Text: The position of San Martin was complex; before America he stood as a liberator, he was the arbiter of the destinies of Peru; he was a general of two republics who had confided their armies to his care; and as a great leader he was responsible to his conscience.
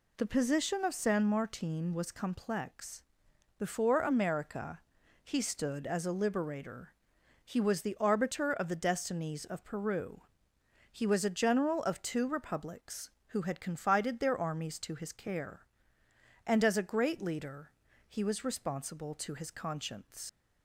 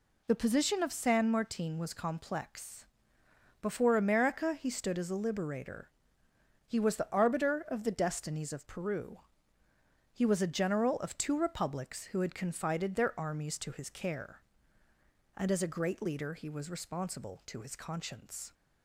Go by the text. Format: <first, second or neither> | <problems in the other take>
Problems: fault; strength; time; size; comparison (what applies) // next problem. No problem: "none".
second | pauses between "America" and "he"; noticeable; at 4.7 s; 0.46 s long // pauses between "leader" and "he"; slight; at 17.7 s; 0.34 s long // leaves "conscience" unfinished; at 20.2 s; 70 ms